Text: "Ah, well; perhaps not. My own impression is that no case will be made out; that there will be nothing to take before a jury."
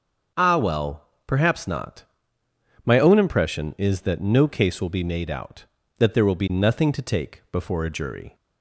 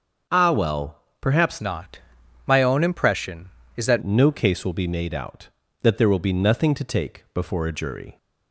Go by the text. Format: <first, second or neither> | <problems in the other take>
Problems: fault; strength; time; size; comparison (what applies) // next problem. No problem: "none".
first | starts louder than the rest; until 1.5 s; 6.5 dB; also in the first // changes voice from "not" to "that"; from 1.5 to 4.0 s; 2.5 s long